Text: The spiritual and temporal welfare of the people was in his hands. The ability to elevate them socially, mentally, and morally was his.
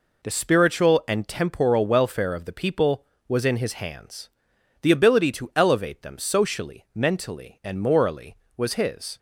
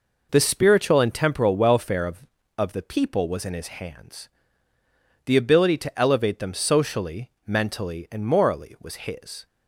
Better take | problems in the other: first | says "of" twice; at 2.5 s

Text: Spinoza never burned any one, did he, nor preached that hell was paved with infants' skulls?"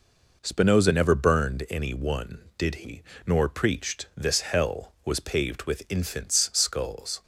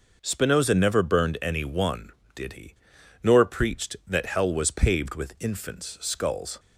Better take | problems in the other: second | says "this" for "that"; at 4.1 s

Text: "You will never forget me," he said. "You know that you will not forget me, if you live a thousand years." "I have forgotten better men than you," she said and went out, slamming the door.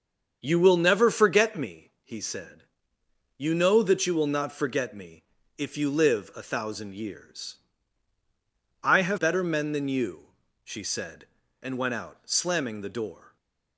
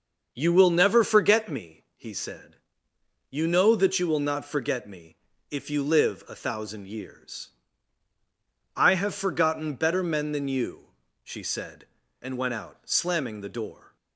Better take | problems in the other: second | starts louder than the rest; until 1.4 s; 7 dB; also in the second // skips "forgotten"; at 9.1 s // stays silent after the last word; slight; from 13.2 s on; 0.5 s long

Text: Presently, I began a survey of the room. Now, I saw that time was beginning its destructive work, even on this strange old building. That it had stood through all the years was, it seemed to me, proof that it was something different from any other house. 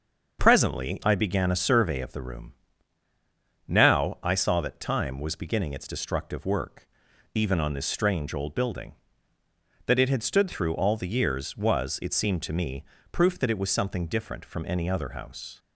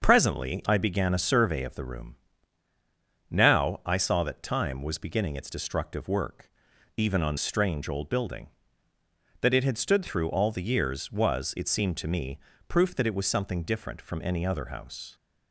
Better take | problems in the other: first | starts louder than the rest; until 1.0 s; 6.5 dB; also in the first // skips "this"; at 7.3 s

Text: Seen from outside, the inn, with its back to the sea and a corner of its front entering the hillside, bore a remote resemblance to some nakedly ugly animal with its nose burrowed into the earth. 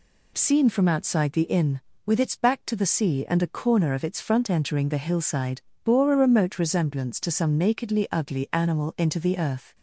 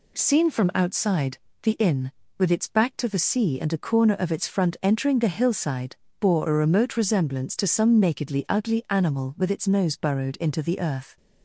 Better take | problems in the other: second | skips "with its nose burrowed"; at 8.9 s

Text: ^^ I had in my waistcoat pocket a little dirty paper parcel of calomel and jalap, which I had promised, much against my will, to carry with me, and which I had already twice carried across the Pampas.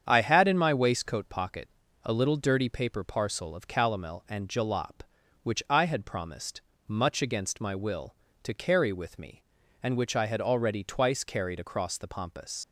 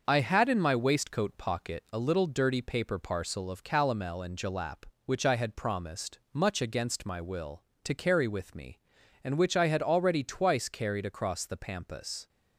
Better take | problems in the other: second | starts louder than the rest; strong; until 1.0 s; 8 dB; also in the second // pauses between "pocket" and "a"; slight; at 1.6 s; 0.36 s long // leaves "Pampas" unfinished; at 12.6 s; 85 ms

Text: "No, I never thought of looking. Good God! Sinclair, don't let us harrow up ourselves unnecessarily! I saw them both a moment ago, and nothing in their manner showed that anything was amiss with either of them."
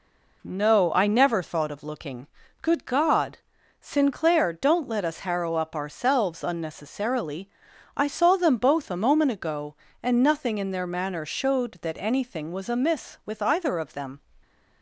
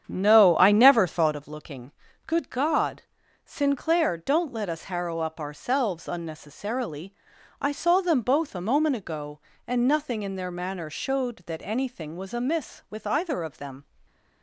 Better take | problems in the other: first | starts louder than the rest; strong; until 1.5 s; 8.5 dB // stays silent after the last word; slight; from 13.8 s on; 0.6 s long

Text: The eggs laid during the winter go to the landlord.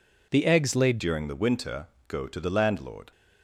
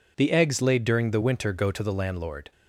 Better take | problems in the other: second | changes voice at "during"; from 0.9 s on; 2.2 s long // pauses between "winter" and "go"; slight; at 1.8 s; 0.20 s long

